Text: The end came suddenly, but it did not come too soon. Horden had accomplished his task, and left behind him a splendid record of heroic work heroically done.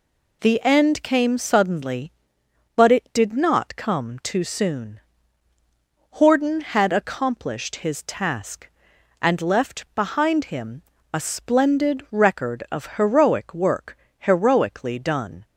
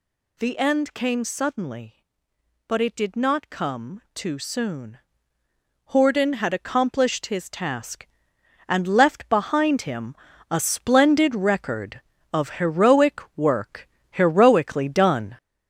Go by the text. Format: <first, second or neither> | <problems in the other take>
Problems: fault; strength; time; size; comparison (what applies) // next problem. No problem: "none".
first | gets louder; noticeable; throughout; 6 dB // pauses between "him" and "a"; at 10.1 s; 0.38 s long; slight in the first // pauses between "heroic" and "work"; slight; at 13.2 s; 0.16 s long // pauses between "work" and "heroically"; slight; at 13.8 s; 0.24 s long; slight in the first